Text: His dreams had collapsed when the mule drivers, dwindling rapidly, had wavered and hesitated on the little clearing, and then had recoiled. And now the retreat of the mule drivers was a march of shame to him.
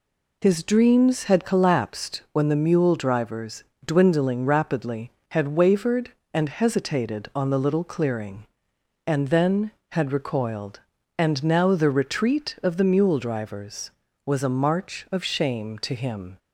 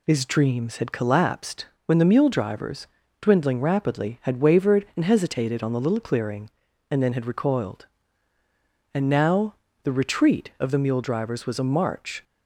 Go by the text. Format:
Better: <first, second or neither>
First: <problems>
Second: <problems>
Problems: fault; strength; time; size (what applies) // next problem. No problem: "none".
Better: first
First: none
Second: pauses between "collapsed" and "when"; slight; at 1.6 s; 0.18 s long // pauses between "now" and "the"; slight; at 9.5 s; 0.28 s long // stops before "of shame to him"; at 12.2 s